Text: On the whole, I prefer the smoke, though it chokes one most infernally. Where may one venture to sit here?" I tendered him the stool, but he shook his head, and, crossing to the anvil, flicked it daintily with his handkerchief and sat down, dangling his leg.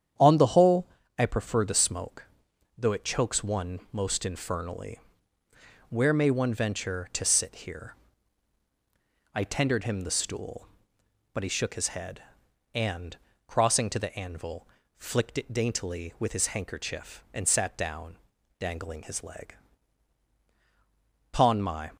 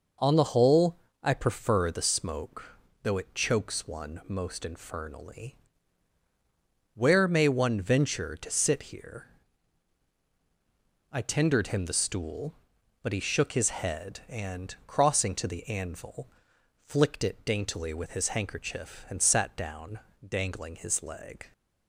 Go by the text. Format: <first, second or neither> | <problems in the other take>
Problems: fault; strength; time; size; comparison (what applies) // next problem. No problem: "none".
second | starts louder than the rest; strong; until 1.4 s; 9 dB // goes on to say "Pon my"; noticeable; from 21.3 s on; 0.64 s long